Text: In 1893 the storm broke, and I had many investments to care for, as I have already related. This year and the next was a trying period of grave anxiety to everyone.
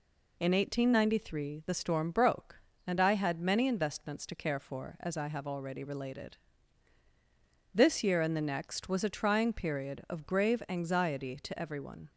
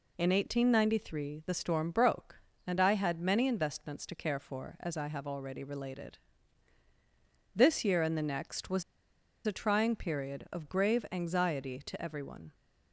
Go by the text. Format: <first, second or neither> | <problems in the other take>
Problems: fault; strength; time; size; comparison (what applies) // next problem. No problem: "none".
first | pauses between "was" and "a"; noticeable; at 8.8 s; 0.63 s long